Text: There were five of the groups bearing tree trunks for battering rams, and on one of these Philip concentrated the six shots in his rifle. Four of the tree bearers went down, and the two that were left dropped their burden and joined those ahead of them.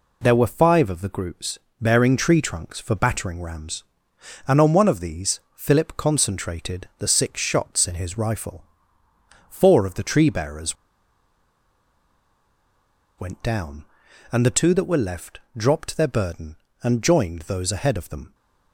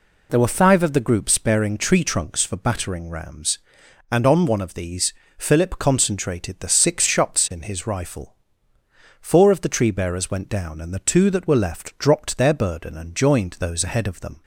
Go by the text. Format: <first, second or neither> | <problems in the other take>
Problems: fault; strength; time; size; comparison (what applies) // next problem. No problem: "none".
second | pauses between "groups" and "bearing"; slight; at 1.5 s; 0.22 s long // pauses between "these" and "Philip"; slight; at 5.4 s; 0.16 s long; slight in the second // pauses between "bearers" and "went"; strong; at 10.7 s; 2.4 s long